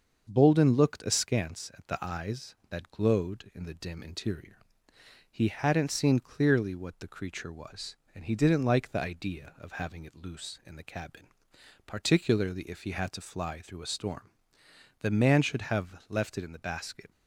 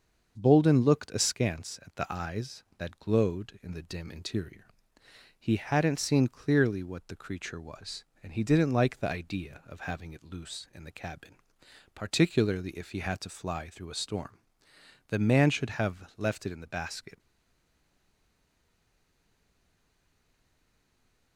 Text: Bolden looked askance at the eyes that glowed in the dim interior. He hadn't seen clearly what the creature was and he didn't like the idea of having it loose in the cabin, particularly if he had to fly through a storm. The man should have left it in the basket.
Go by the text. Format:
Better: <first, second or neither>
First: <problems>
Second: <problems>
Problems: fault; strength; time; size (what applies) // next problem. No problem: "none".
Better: first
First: starts louder than the rest; until 1.3 s; 6.5 dB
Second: starts louder than the rest; until 1.4 s; 6.5 dB // stays silent after the last word; strong; from 17.1 s on; 4.2 s long